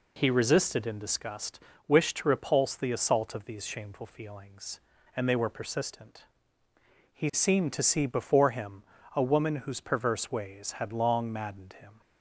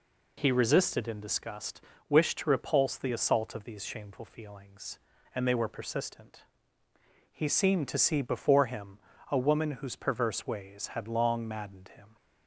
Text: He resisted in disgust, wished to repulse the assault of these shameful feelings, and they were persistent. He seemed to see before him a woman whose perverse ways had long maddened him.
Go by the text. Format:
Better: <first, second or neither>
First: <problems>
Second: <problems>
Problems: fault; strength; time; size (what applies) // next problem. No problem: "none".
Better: neither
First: pauses between "him" and "a"; slight; at 8.8 s; 0.34 s long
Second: pauses between "him" and "a"; slight; at 8.9 s; 0.34 s long